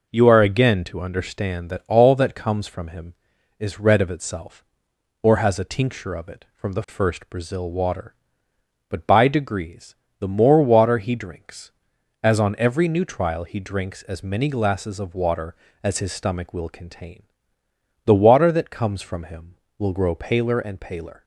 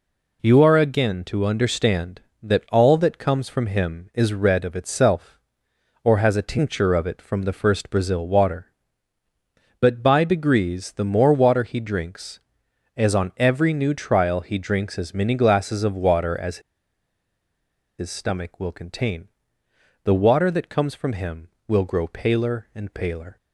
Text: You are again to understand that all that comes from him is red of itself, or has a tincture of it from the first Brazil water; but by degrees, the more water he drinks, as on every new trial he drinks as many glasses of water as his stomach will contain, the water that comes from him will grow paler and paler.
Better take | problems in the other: first | pauses between "as" and "his"; strong; at 16.6 s; 1.3 s long

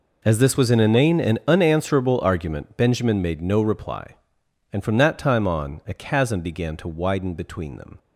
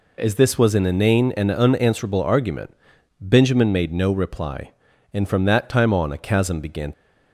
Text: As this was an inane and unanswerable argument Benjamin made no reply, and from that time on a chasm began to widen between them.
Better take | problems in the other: first | pauses between "argument" and "Benjamin"; noticeable; at 2.7 s; 0.46 s long // stops before "to widen between them"; at 6.9 s

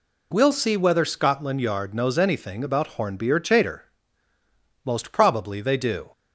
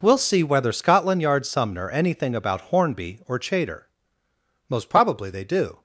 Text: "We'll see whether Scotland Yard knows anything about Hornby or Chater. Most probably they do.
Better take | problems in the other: first | says "sumner" for "knows"; at 1.4 s

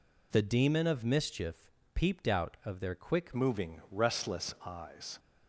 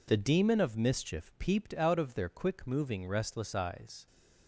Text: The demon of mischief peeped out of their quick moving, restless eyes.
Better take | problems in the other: second | pauses between "mischief" and "peeped"; slight; at 1.6 s; 0.24 s long // changes voice at "moving"; from 3.3 s on; 1.8 s long

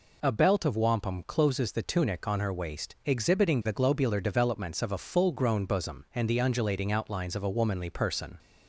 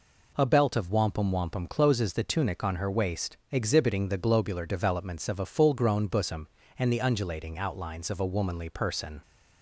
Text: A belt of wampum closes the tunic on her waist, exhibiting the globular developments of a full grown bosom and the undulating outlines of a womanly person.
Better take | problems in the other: first | says "wampum" twice; at 1.2 s

